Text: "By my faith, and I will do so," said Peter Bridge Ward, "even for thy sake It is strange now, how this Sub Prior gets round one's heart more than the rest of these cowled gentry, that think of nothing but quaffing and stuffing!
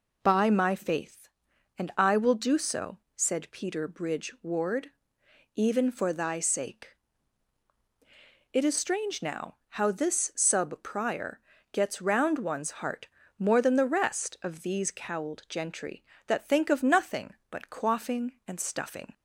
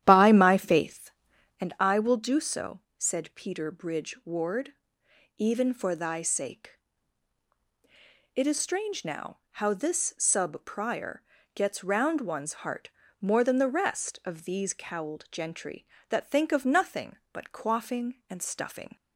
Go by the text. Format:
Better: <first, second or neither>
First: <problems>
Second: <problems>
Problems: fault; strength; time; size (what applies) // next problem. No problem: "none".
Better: first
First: pauses between "sake" and "It"; strong; at 6.9 s; 1.5 s long // pauses between "Prior" and "gets"; slight; at 11.3 s; 0.32 s long // pauses between "heart" and "more"; slight; at 13.0 s; 0.30 s long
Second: starts louder than the rest; strong; until 1.7 s; 11 dB // pauses between "sake" and "It"; strong; at 6.7 s; 1.5 s long // pauses between "Prior" and "gets"; slight; at 11.2 s; 0.32 s long // pauses between "heart" and "more"; slight; at 12.8 s; 0.30 s long